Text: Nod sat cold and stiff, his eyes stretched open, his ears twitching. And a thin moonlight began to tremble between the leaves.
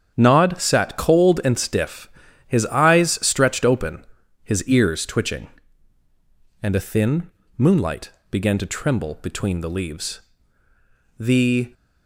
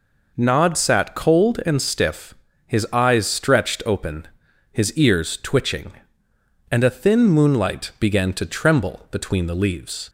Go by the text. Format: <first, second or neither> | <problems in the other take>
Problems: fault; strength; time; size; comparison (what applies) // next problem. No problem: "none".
second | starts louder than the rest; strong; until 1.1 s; 8 dB // pauses between "thin" and "moonlight"; slight; at 7.3 s; 0.26 s long // pauses between "moonlight" and "began"; slight; at 8.1 s; 0.18 s long // goes on to say "The"; from 11.1 s on; 0.54 s long